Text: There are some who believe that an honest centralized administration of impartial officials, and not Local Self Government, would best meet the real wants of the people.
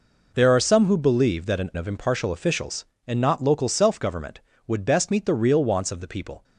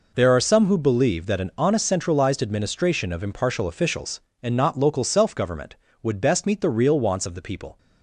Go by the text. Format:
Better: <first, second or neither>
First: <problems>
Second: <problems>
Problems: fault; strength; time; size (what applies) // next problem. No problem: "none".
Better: second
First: skips "honest centralized administration"; at 1.7 s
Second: none